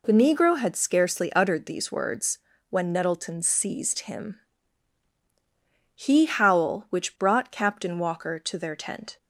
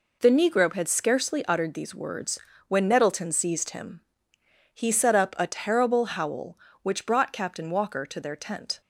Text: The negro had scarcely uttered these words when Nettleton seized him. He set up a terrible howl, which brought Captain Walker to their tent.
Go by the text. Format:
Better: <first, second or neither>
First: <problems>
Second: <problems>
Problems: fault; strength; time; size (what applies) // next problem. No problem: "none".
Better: second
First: pauses between "words" and "when"; slight; at 2.3 s; 0.32 s long // skips "set up a terrible"; at 6.2 s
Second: pauses between "words" and "when"; slight; at 2.3 s; 0.30 s long